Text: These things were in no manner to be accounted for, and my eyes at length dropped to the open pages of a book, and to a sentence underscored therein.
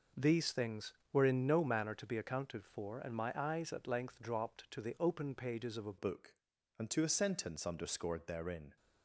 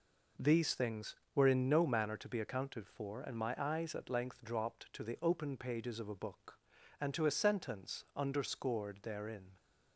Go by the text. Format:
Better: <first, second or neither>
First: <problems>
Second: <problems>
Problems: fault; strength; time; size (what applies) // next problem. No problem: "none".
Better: second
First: changes voice at "book"; from 5.9 s on; 2.8 s long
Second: none